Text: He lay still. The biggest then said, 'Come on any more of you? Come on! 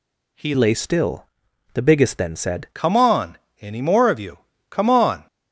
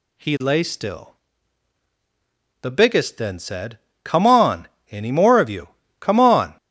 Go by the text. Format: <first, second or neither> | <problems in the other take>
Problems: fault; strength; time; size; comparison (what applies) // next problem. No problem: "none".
second | changes voice from "lay" to "said"; from 0.5 to 2.6 s; 2.1 s long // pauses between "on" and "any"; slight; at 3.3 s; 0.24 s long; slight in the second